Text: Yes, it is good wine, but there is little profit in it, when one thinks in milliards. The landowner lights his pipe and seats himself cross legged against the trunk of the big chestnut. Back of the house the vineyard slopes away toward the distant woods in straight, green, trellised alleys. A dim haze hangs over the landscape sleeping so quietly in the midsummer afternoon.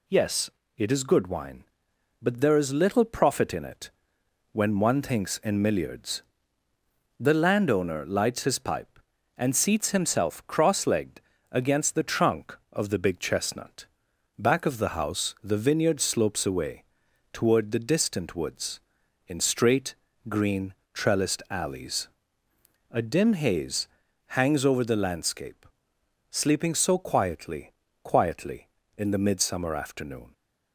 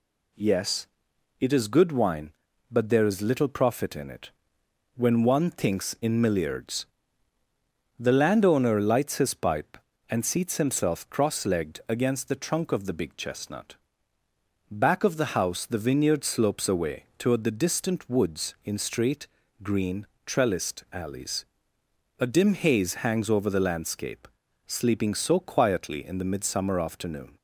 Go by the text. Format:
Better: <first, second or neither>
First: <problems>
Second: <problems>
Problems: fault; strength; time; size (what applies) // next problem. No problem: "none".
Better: second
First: pauses between "legged" and "against"; slight; at 11.2 s; 0.30 s long // pauses between "away" and "toward"; noticeable; at 16.8 s; 0.48 s long // pauses between "haze" and "hangs"; noticeable; at 23.8 s; 0.48 s long // pauses between "landscape" and "sleeping"; noticeable; at 25.6 s; 0.64 s long // says "quietly" twice; at 28.0 s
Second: pauses between "landscape" and "sleeping"; at 24.2 s; 0.38 s long